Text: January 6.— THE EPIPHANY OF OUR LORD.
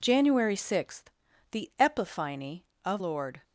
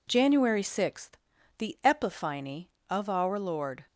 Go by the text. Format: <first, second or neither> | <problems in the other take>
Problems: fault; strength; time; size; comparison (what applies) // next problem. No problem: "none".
second | skips "OUR"; at 3.0 s